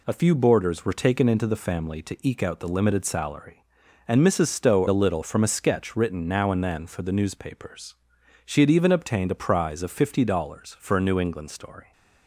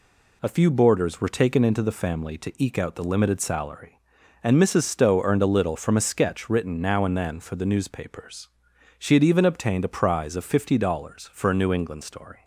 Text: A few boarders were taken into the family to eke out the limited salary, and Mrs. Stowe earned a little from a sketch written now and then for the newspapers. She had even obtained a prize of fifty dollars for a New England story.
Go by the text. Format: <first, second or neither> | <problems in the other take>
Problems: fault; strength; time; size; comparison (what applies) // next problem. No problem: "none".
second | skips "earned"; at 4.8 s